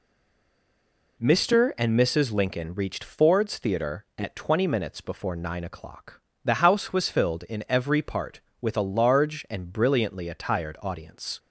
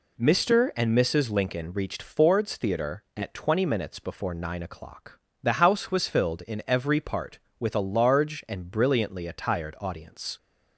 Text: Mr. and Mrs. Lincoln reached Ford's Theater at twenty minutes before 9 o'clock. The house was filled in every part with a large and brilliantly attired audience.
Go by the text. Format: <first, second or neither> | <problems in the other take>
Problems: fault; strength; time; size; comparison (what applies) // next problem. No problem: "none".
second | stays silent before the first word; noticeable; until 1.1 s; 1.1 s long